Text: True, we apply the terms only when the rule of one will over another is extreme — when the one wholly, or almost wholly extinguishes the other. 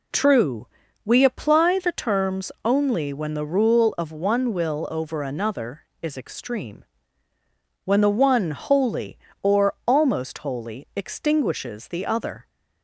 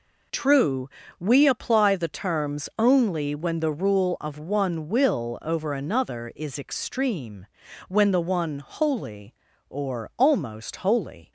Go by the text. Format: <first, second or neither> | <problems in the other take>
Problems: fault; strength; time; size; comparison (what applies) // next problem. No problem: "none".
first | stops before "extinguishes the other"; at 11.2 s